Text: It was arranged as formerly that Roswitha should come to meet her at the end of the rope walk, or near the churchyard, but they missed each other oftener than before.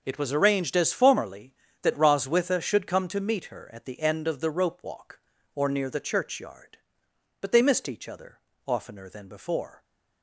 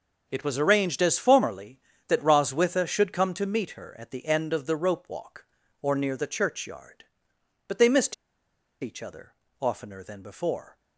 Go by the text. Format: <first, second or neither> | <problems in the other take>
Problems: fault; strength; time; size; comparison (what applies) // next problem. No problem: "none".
first | pauses between "missed" and "each"; noticeable; at 8.1 s; 0.67 s long // pauses between "other" and "oftener"; slight; at 9.3 s; 0.28 s long; slight in the first